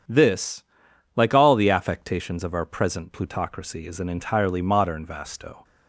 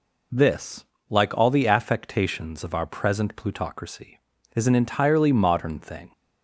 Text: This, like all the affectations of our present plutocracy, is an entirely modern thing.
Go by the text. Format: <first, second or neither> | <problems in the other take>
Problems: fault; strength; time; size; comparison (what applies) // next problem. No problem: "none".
second | starts louder than the rest; strong; until 1.6 s; 8 dB // says "vasto" for "thing"; at 5.0 s